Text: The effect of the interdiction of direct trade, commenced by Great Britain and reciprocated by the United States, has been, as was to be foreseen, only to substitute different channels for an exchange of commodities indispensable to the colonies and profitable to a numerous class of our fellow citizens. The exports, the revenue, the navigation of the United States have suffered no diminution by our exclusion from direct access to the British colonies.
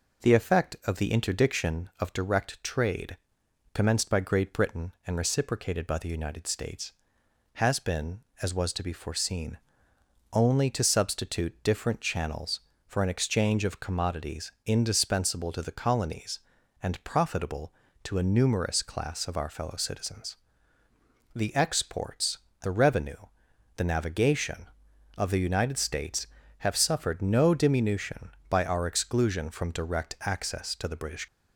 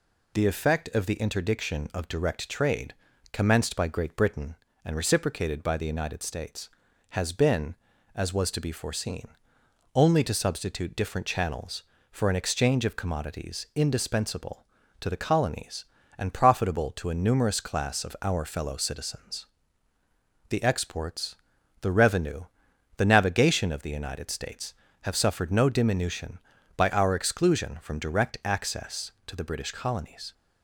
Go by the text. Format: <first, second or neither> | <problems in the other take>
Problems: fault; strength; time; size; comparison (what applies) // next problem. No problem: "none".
second | stops before "colonies"; at 31.2 s